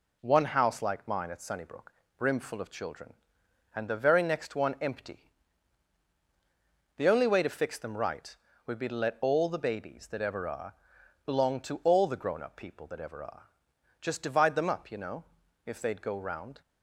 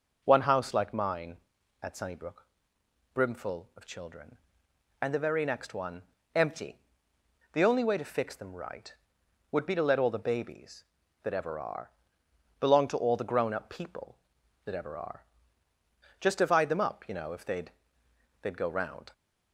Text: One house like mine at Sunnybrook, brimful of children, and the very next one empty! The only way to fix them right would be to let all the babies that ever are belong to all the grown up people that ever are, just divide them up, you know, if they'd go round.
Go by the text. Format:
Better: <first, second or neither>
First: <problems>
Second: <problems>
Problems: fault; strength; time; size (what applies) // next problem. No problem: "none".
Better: first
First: pauses between "are" and "belong"; noticeable; at 10.7 s; 0.52 s long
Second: pauses between "one" and "empty"; slight; at 6.0 s; 0.32 s long // pauses between "are" and "belong"; noticeable; at 11.9 s; 0.70 s long // says "they'd" twice; at 18.4 s